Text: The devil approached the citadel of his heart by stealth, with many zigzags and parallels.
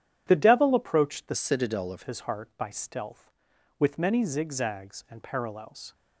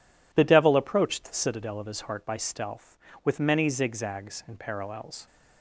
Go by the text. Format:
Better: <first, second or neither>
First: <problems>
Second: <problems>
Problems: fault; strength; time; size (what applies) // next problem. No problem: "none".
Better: second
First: starts louder than the rest; strong; until 1.2 s; 10.5 dB // changes voice from "citadel" to "of"; from 1.3 to 2.0 s; 0.7 s long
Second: none